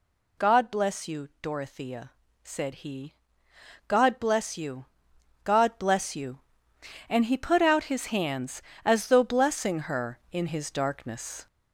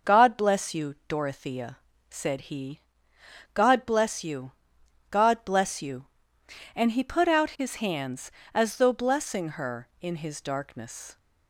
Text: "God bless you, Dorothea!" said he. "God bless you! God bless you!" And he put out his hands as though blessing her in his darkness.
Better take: second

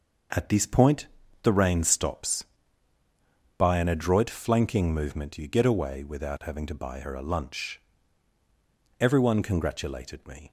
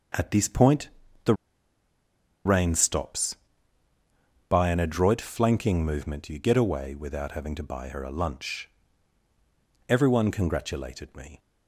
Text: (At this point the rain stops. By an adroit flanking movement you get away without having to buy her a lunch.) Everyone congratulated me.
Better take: first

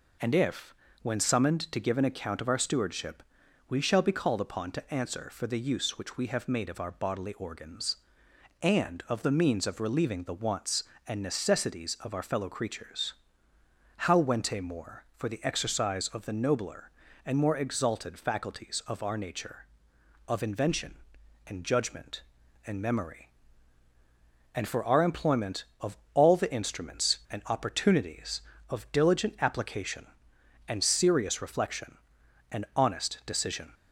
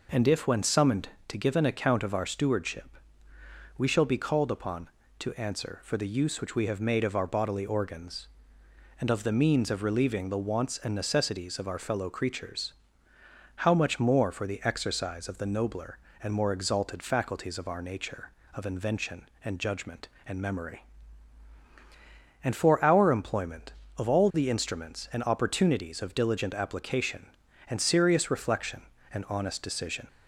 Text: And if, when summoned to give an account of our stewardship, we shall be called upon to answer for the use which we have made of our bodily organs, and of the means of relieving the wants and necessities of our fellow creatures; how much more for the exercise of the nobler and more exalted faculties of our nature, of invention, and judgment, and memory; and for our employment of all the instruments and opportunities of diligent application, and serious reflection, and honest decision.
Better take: second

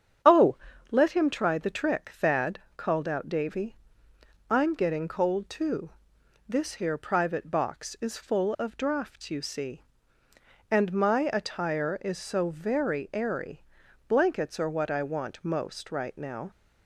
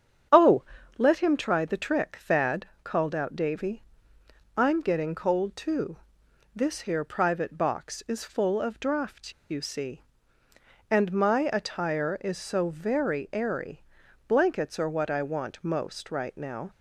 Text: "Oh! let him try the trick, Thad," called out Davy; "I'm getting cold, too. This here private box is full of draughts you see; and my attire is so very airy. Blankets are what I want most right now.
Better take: first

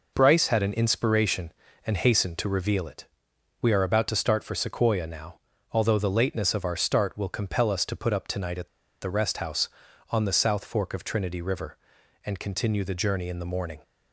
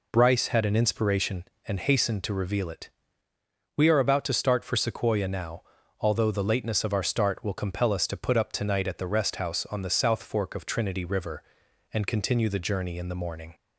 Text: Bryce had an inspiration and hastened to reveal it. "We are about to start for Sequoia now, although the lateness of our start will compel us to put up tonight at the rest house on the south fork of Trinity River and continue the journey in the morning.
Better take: second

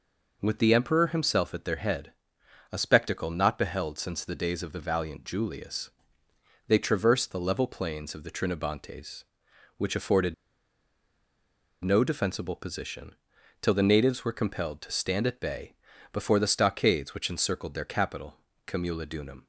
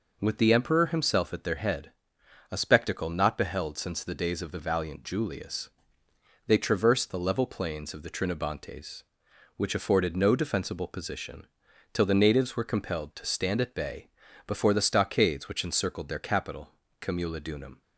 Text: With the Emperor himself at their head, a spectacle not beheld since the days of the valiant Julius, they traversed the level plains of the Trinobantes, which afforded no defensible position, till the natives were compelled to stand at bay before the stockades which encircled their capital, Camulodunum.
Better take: second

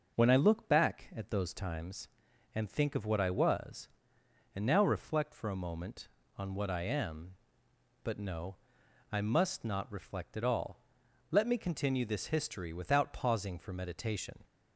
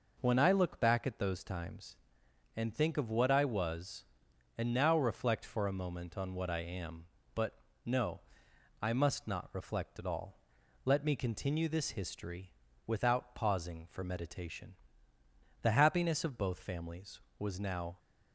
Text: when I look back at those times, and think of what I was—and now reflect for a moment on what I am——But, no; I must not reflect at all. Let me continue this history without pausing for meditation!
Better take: first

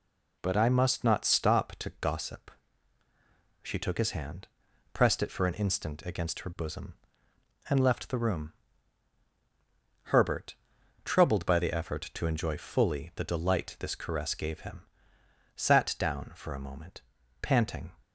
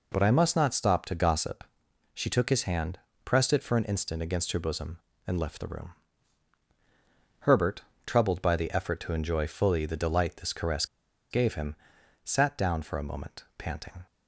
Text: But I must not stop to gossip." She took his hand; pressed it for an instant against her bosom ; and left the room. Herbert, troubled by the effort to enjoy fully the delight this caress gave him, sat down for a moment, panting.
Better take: first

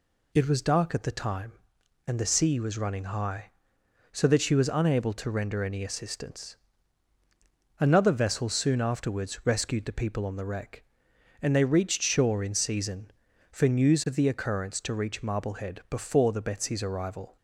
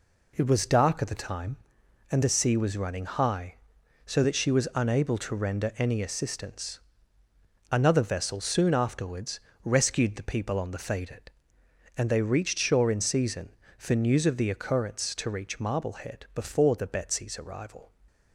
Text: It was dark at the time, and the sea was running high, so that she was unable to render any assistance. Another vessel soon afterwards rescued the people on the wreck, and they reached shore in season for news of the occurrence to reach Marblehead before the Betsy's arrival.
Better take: first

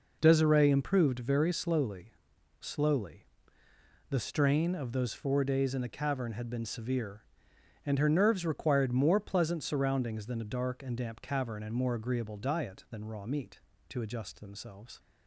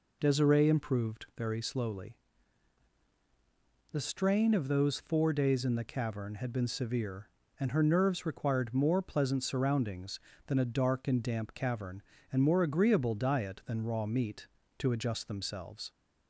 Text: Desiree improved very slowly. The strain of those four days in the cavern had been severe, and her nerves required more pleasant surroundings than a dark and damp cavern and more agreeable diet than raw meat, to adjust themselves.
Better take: second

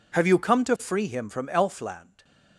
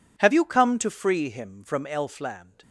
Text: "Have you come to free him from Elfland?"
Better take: neither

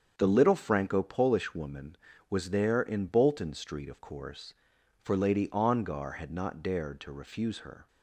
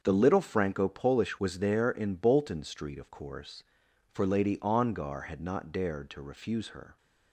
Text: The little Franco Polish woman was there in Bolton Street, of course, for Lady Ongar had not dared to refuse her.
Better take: first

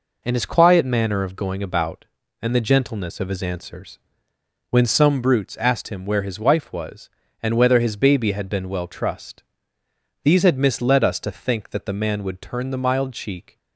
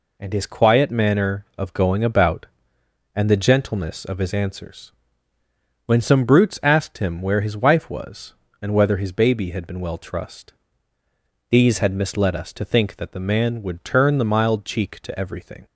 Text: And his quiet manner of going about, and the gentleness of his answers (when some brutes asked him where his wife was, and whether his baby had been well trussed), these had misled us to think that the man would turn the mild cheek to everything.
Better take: second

